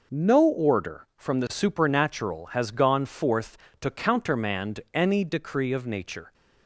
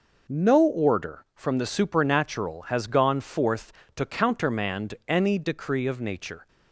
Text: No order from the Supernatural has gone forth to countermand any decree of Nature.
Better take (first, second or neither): neither